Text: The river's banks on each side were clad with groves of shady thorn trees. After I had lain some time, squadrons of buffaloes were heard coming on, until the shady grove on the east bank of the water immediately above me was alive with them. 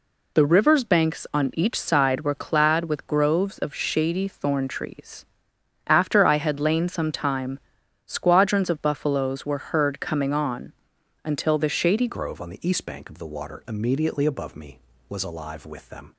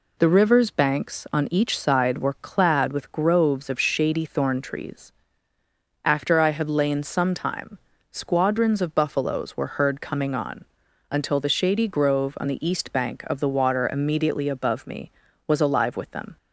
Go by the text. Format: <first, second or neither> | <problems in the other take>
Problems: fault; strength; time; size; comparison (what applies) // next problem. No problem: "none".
second | changes voice at "grove"; from 12.0 s on; 4.1 s long